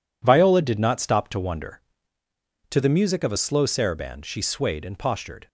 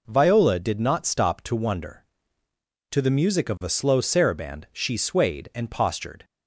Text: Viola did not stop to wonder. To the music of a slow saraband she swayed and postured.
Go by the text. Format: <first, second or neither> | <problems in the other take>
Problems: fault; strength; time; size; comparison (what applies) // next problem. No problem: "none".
neither | none